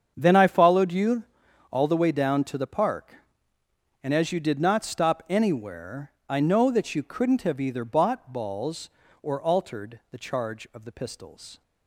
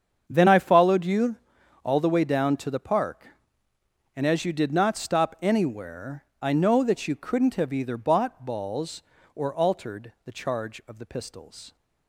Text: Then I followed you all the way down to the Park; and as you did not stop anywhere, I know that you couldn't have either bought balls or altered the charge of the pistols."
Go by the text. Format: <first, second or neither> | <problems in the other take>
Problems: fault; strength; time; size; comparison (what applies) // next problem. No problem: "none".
neither | starts louder than the rest; strong; the same in both // pauses between "you" and "all"; noticeable; the same in both